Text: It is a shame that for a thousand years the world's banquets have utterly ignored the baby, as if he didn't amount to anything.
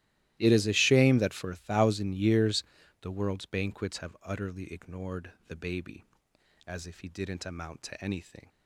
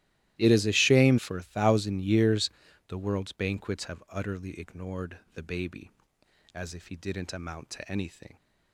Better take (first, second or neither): first